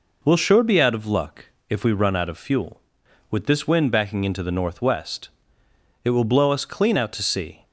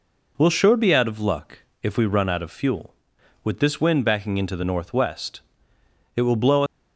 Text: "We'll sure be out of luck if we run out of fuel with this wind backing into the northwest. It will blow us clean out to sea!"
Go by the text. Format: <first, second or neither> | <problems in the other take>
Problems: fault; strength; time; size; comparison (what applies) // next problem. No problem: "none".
first | pauses between "luck" and "if"; slight; at 1.5 s; 0.22 s long; slight in the first // stops before "us clean out to sea"; at 6.6 s